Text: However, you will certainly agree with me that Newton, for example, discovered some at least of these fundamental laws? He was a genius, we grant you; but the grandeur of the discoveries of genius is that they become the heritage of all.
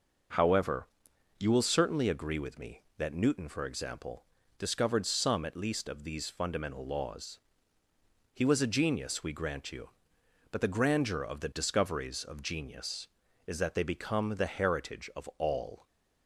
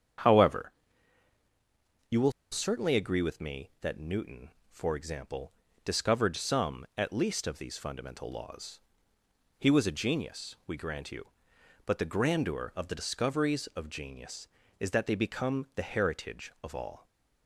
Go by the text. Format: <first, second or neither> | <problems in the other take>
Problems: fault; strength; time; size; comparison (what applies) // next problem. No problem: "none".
first | starts louder than the rest; strong; until 2.7 s; 8 dB // pauses between "will" and "certainly"; slight; at 2.3 s; 0.20 s long